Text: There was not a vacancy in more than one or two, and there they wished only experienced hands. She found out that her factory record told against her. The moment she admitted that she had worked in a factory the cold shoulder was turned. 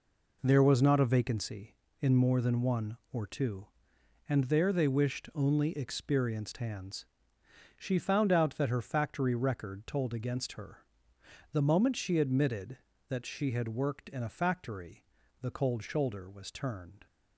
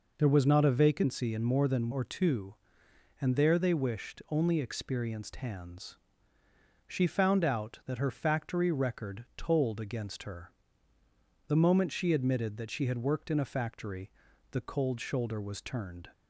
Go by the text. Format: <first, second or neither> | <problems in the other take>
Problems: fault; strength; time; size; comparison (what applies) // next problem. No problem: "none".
first | skips "one"; at 1.9 s // pauses between "factory" and "the"; at 14.1 s; 0.40 s long; slight in the first